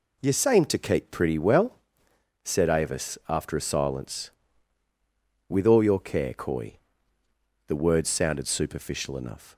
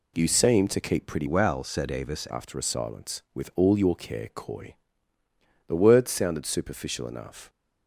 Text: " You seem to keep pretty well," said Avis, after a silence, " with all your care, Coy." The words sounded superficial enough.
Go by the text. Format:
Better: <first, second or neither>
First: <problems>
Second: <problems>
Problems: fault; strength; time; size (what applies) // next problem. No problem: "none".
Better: first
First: none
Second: changes voice from "well" to "Avis"; from 1.2 to 2.2 s; 1.0 s long